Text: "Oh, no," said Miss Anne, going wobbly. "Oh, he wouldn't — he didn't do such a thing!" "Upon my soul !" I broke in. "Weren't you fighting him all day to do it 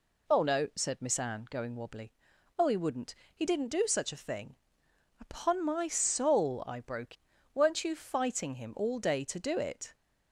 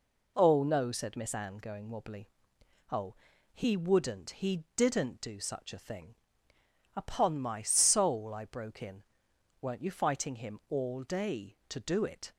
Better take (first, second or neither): second